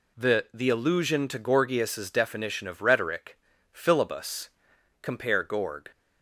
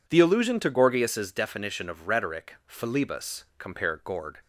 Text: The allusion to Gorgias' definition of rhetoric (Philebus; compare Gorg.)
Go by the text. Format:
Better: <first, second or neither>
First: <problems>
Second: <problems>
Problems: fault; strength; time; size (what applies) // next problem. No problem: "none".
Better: second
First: says "The" twice; at 0.5 s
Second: none